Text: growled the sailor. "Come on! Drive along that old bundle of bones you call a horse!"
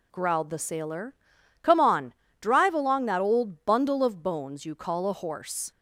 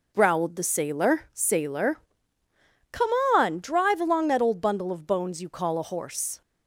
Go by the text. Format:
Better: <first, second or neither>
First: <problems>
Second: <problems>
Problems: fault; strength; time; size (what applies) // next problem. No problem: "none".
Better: first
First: none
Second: says "sailor" twice; at 1.3 s